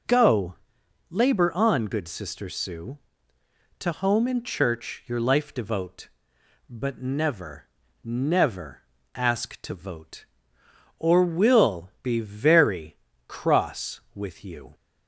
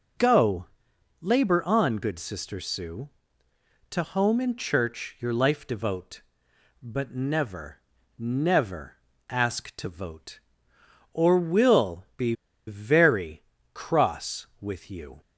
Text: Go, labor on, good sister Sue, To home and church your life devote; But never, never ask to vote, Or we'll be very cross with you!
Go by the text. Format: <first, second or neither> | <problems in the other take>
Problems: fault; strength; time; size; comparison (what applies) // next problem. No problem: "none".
first | pauses between "never" and "ask"; slight; at 8.9 s; 0.34 s long; slight in the first // pauses between "be" and "very"; slight; at 12.3 s; 0.34 s long // pauses between "very" and "cross"; slight; at 13.4 s; 0.32 s long; slight in the first